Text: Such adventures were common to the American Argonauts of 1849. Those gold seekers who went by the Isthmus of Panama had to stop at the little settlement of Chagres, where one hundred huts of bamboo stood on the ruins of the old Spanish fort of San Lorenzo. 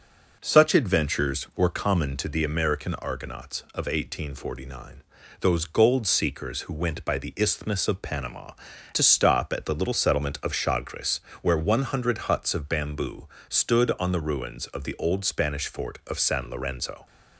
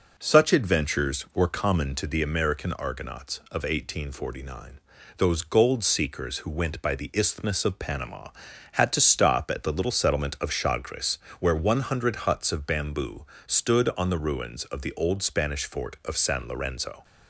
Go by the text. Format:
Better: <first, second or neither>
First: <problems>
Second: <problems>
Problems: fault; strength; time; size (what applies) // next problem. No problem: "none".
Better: second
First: skips "had"; at 8.7 s // pauses between "bamboo" and "stood"; slight; at 13.2 s; 0.20 s long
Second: pauses between "bamboo" and "stood"; slight; at 13.2 s; 0.20 s long